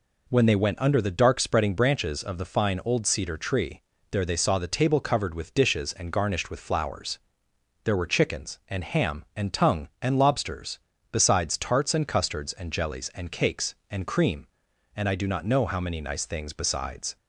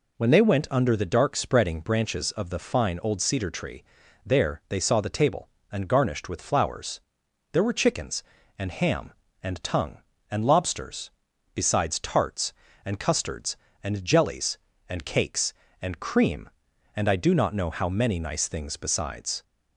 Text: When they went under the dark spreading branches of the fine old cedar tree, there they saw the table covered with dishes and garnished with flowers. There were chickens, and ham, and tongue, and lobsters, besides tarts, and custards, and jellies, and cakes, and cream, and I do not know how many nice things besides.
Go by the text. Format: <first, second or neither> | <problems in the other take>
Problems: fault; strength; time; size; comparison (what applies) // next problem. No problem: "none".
first | skips "covered with dishes"; at 5.5 s